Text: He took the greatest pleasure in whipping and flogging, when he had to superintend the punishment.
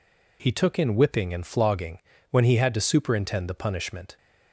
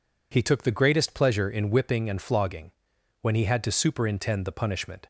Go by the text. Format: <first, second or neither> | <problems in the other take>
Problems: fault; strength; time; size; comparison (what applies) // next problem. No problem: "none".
second | skips "the greatest pleasure"; at 0.7 s